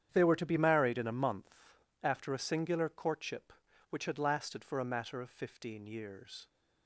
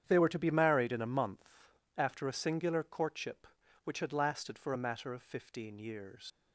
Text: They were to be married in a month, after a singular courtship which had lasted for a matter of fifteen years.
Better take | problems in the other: first | starts louder than the rest; strong; until 1.0 s; 9 dB; strong in the first // leaves "years" unfinished; at 6.3 s; 110 ms

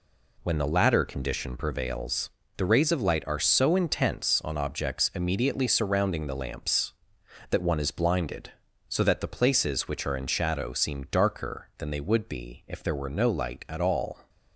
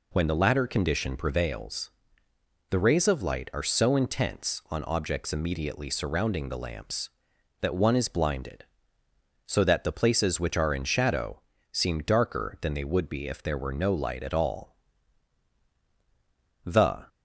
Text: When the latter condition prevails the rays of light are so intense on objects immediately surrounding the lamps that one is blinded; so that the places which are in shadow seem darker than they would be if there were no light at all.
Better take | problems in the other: first | pauses between "prevails" and "the"; noticeable; at 1.8 s; 0.80 s long; slight in the first // pauses between "shadow" and "seem"; slight; at 11.4 s; 0.32 s long // goes on to say "The"; slight; from 16.6 s on; 0.40 s long

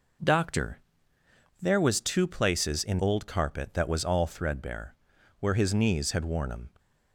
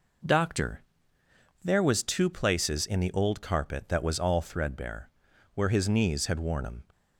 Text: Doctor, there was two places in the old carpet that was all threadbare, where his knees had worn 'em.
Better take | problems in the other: second | skips "the"; at 2.9 s

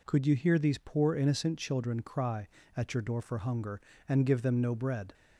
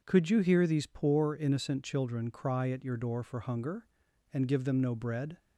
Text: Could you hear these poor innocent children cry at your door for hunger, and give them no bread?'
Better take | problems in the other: neither | none

